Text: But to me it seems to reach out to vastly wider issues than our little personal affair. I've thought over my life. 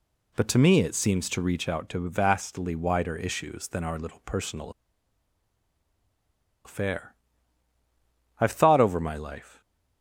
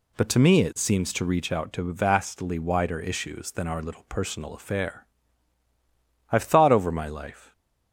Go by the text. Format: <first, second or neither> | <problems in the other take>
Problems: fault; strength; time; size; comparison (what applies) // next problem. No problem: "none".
second | pauses between "personal" and "affair"; strong; at 4.7 s; 1.9 s long